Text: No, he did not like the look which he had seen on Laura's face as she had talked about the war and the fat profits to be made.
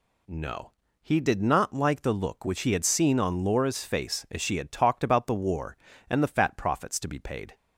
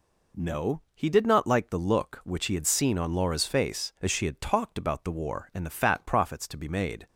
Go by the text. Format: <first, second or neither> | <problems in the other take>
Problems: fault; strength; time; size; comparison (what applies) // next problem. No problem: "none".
second | says "paid" for "made"; at 7.1 s